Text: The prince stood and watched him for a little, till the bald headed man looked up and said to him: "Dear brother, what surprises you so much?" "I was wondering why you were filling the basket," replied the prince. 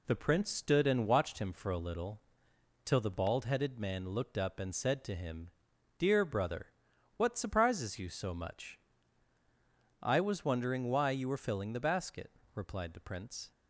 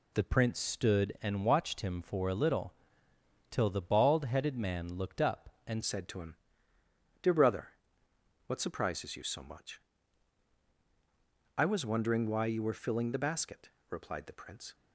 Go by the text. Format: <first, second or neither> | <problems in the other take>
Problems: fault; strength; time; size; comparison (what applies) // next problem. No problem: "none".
first | changes voice at "said"; from 5.8 s on; 8.9 s long